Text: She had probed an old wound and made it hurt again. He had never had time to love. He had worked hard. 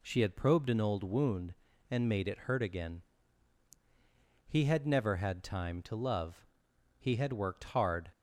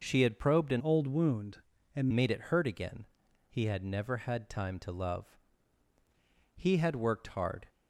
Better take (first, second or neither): first